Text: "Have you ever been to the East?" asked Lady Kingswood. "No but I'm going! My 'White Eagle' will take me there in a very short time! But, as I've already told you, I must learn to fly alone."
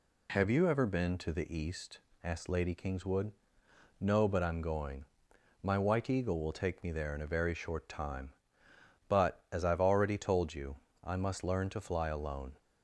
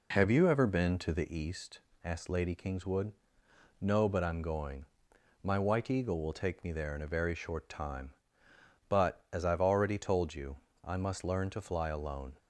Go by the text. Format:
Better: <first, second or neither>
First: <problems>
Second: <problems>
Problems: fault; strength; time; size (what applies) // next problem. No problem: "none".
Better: first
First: none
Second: starts louder than the rest; until 1.4 s; 3.5 dB